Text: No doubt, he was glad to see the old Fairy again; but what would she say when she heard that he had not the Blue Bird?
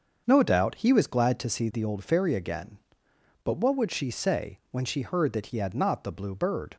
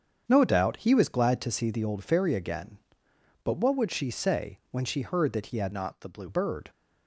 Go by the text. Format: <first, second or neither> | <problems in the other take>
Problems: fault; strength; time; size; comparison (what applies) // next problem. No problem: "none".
first | starts louder than the rest; strong; until 1.2 s; 7.5 dB; also in the first // changes voice from "not" to "Blue"; from 5.7 to 6.2 s; 0.5 s long